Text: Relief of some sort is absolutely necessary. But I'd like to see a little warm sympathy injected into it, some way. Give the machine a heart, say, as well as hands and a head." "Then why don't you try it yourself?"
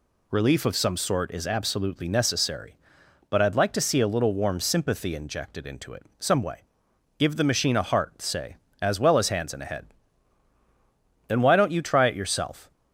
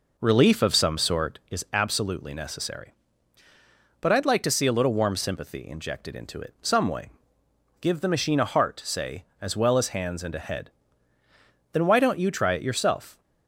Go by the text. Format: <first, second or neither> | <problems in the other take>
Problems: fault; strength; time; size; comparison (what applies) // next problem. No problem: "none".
first | starts louder than the rest; noticeable; until 1.4 s; 4.5 dB